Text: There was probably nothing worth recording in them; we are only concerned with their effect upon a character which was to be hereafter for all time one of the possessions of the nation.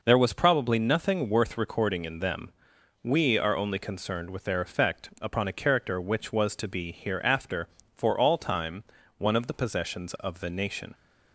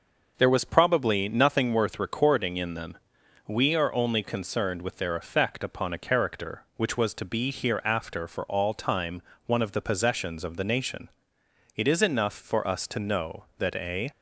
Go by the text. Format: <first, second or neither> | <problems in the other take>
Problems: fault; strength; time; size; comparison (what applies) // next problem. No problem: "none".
first | pauses between "time" and "one"; slight; at 9.2 s; 0.26 s long; slight in the first // goes on to say "It is enough for us to know that a"; strong; from 11.7 s on; 2.3 s long